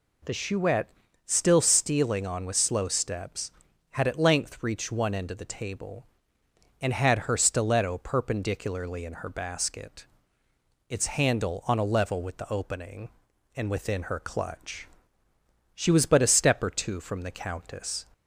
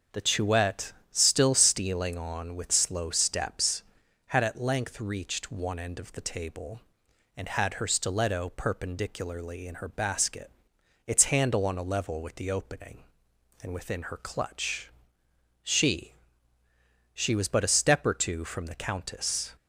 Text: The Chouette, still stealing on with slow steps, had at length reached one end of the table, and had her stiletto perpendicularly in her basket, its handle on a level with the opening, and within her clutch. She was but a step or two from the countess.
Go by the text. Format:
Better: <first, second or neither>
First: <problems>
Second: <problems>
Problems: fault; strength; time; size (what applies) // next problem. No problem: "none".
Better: first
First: none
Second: starts louder than the rest; until 1.3 s; 7 dB // says "She" twice; at 17.1 s